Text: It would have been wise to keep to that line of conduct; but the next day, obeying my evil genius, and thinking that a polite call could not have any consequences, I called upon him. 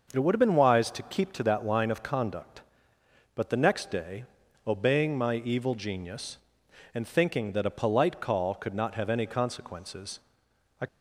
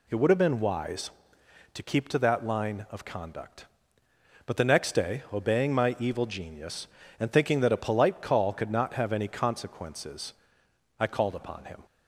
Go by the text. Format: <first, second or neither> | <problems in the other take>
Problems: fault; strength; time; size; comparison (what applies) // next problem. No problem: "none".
second | starts louder than the rest; noticeable; until 1.1 s; 6 dB // stops before "called upon him"; at 10.8 s